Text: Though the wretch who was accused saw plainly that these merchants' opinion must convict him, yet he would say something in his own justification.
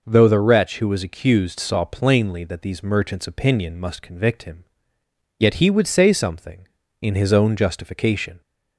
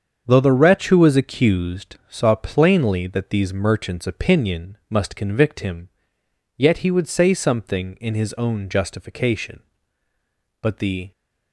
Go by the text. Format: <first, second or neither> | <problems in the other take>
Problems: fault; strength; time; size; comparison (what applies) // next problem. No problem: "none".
first | starts louder than the rest; strong; until 1.2 s; 7 dB // goes on to say "But the"; from 10.6 s on; 0.50 s long